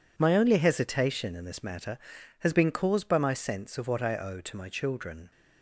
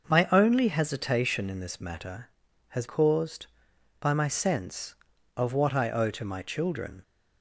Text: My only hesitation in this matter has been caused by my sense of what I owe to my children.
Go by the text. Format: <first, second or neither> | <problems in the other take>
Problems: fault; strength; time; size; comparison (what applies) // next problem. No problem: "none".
first | starts louder than the rest; noticeable; until 1.0 s; 6 dB // skips "been"; at 2.8 s